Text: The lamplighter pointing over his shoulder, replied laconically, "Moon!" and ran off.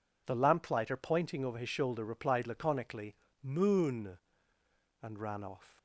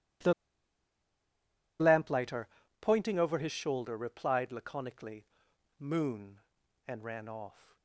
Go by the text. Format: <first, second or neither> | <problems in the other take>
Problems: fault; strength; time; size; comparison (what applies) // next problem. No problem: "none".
first | pauses between "The" and "lamplighter"; strong; at 0.3 s; 1.4 s long // pauses between "lamplighter" and "pointing"; slight; at 2.4 s; 0.32 s long